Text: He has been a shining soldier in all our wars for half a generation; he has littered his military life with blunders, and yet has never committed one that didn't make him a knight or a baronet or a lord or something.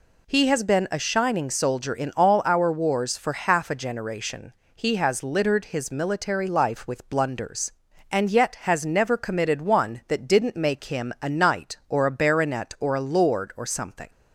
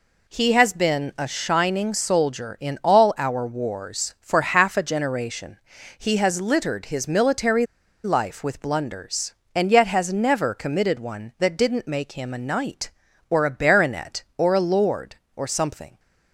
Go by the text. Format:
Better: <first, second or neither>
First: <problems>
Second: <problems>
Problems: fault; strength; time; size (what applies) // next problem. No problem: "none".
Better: first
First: none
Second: pauses between "military" and "life"; at 7.6 s; 0.38 s long